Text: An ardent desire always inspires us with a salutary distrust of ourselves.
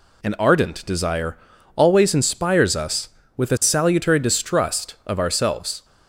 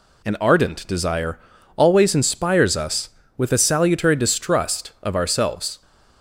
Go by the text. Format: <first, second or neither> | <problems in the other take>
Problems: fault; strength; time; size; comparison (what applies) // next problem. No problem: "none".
neither | pauses between "desire" and "always"; the same in both